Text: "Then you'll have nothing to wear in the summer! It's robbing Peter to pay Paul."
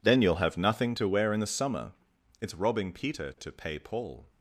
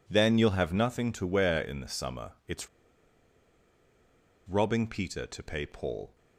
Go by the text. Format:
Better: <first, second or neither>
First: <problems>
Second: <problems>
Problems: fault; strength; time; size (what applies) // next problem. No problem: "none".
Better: first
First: none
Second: pauses between "It's" and "robbing"; strong; at 2.6 s; 1.8 s long